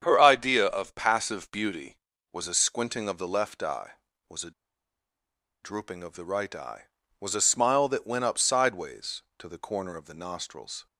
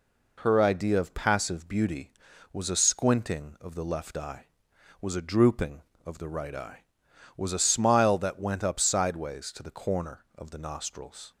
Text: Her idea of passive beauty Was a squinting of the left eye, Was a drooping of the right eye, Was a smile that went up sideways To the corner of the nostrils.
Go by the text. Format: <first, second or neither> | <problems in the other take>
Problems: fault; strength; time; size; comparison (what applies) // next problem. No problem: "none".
second | starts louder than the rest; strong; until 1.0 s; 8 dB // pauses between "a" and "drooping"; at 4.5 s; 1.1 s long